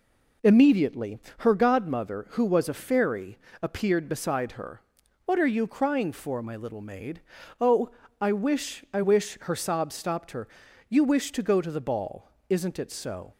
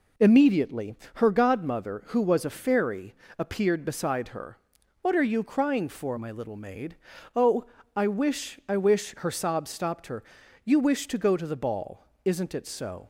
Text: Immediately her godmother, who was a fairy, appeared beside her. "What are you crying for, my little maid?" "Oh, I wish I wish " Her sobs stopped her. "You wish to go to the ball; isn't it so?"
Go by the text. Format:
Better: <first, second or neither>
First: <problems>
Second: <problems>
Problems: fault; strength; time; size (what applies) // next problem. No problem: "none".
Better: neither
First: pauses between "Immediately" and "her"; slight; at 1.1 s; 0.20 s long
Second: pauses between "Immediately" and "her"; slight; at 0.9 s; 0.20 s long